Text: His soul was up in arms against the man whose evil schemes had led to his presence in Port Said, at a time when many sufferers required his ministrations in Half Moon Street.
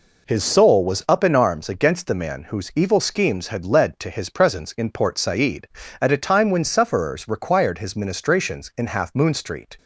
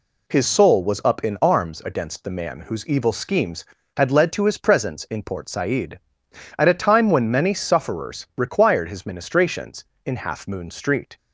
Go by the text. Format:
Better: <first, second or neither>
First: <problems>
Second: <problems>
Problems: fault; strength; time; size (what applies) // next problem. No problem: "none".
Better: second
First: skips "many"; at 6.6 s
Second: none